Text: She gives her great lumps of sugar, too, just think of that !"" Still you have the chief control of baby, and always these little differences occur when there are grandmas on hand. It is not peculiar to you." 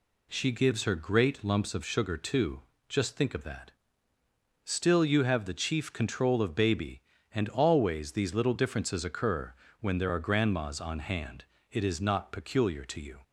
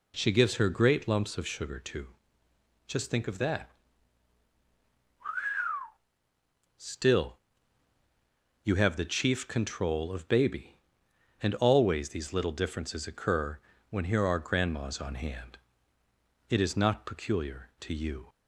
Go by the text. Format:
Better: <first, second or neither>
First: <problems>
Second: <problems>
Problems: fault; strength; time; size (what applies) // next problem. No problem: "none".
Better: first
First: pauses between "occur" and "when"; slight; at 9.5 s; 0.26 s long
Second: pauses between "Still" and "you"; strong; at 7.3 s; 1.2 s long // pauses between "occur" and "when"; slight; at 13.5 s; 0.32 s long // says "here" for "there"; at 14.0 s